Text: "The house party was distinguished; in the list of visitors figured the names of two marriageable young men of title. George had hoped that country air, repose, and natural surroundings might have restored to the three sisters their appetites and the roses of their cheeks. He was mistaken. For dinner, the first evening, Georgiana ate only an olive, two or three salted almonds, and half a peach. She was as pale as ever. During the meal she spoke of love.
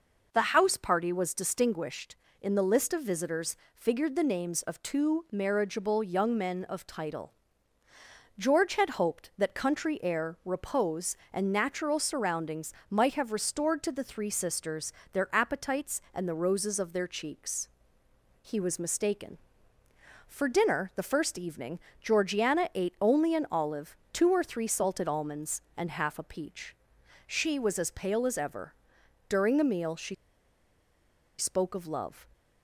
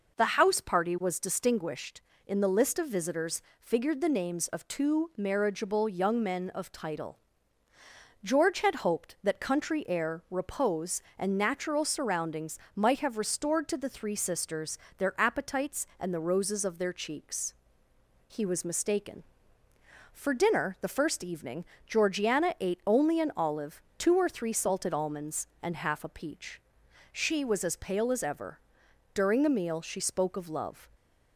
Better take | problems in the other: second | pauses between "visitors" and "figured"; slight; at 3.5 s; 0.18 s long; slight in the second // pauses between "surroundings" and "might"; slight; at 12.7 s; 0.16 s long; slight in the second // pauses between "sisters" and "their"; slight; at 14.9 s; 0.20 s long; slight in the second // pauses between "she" and "spoke"; strong; at 30.1 s; 1.2 s long

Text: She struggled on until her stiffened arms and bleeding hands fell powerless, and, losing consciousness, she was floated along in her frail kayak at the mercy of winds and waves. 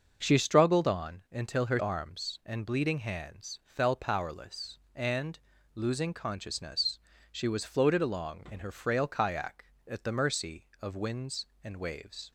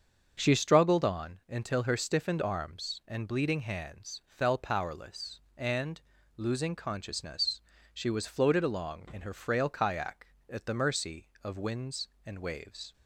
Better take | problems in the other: second | starts louder than the rest; noticeable; until 1.2 s; 6 dB; also in the second // skips "stiffened"; at 1.7 s

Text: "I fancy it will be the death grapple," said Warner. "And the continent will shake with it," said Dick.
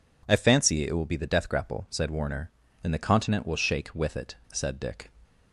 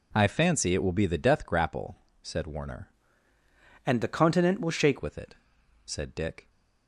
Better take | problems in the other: first | changes voice from "And" to "shake"; from 3.8 to 4.9 s; 1.1 s long

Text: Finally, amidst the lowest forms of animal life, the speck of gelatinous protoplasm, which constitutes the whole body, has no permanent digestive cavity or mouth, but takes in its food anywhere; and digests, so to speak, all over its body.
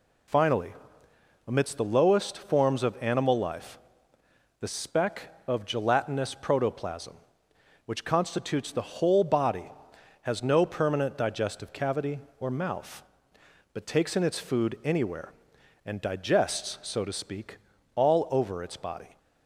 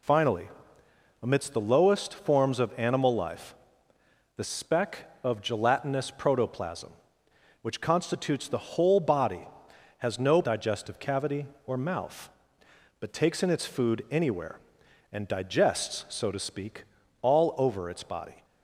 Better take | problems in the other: first | skips "permanent"; at 10.4 s

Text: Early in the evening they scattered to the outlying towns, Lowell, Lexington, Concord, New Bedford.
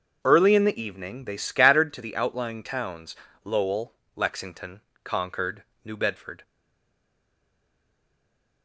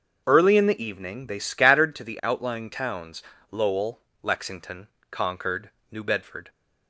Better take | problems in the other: second | starts louder than the rest; until 1.2 s; 6.5 dB; also in the second // stays silent after the last word; from 6.4 s on; 2.2 s long

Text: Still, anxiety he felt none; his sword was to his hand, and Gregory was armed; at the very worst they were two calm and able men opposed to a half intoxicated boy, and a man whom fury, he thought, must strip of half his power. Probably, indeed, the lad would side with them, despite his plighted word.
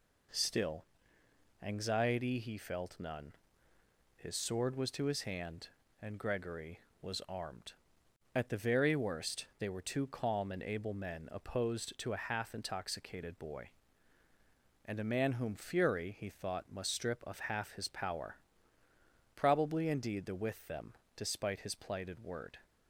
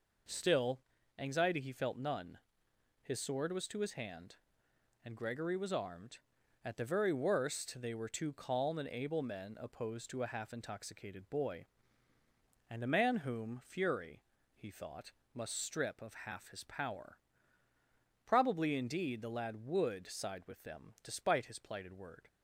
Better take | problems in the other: second | skips "lad would side"; at 20.3 s

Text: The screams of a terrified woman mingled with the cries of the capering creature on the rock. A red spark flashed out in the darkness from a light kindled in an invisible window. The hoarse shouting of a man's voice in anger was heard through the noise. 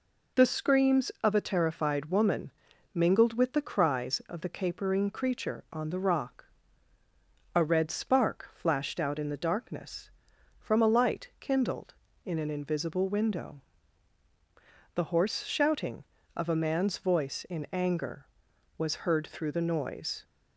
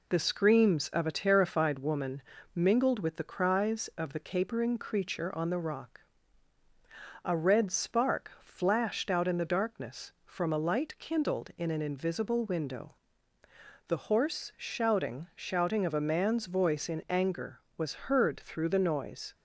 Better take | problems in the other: first | pauses between "woman" and "mingled"; slight; at 2.2 s; 0.32 s long; also in the first // says "shouting" twice; at 15.3 s

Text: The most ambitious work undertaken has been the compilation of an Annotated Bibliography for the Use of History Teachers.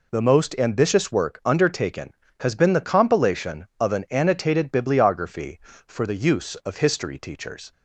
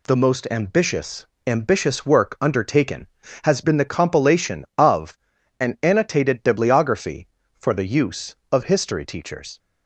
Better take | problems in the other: first | says "ambitious" twice; at 1.4 s // pauses between "of" and "an"; at 5.1 s; 0.44 s long

